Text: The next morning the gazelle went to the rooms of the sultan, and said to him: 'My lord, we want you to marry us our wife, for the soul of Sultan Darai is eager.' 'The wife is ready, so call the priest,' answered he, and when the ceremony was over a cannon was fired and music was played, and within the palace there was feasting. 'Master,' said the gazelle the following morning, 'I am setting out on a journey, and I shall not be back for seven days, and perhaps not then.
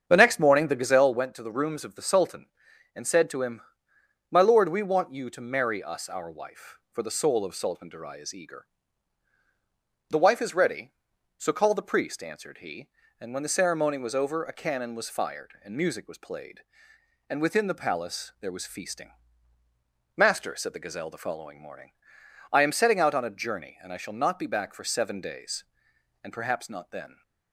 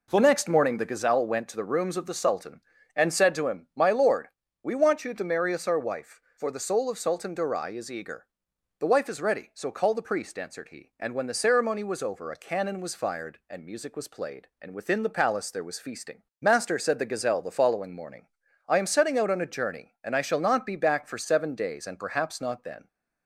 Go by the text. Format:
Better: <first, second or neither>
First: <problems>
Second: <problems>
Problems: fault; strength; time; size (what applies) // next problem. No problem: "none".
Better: second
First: starts louder than the rest; strong; until 1.1 s; 7.5 dB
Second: none